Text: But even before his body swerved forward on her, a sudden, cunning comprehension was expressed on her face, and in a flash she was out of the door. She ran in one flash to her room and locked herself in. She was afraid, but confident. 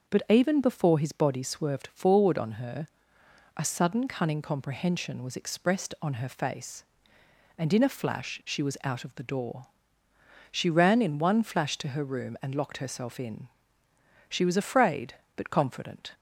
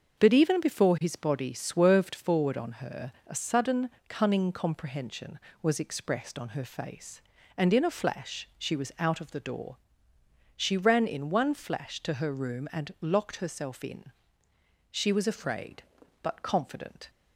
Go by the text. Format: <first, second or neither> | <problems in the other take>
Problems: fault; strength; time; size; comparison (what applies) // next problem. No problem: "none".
neither | starts louder than the rest; the same in both